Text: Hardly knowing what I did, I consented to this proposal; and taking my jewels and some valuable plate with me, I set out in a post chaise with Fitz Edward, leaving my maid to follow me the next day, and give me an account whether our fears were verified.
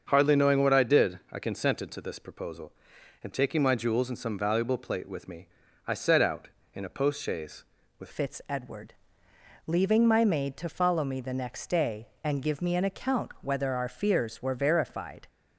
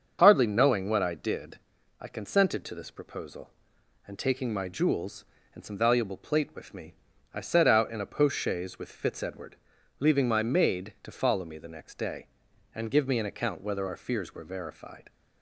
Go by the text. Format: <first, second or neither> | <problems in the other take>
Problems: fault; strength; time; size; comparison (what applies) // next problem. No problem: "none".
second | starts louder than the rest; until 1.0 s; 6.5 dB; also in the second // changes voice at "Fitz"; from 8.1 s on; 7.1 s long